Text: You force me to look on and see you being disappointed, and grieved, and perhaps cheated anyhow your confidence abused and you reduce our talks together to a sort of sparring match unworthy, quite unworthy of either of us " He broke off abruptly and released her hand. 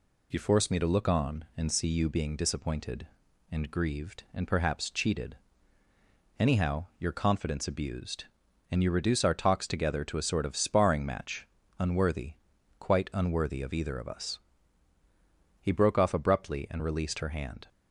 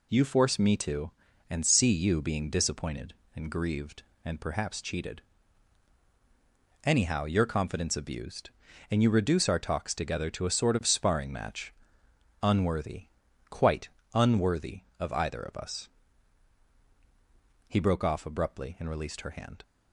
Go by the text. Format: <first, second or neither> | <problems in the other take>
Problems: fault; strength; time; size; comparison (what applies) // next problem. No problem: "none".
first | skips "look on"; at 1.3 s // pauses between "cheated" and "anyhow"; strong; at 5.2 s; 1.6 s long; also in the first // pauses between "match" and "unworthy"; noticeable; at 11.7 s; 0.68 s long; slight in the first // pauses between "quite" and "unworthy"; slight; at 13.9 s; 0.24 s long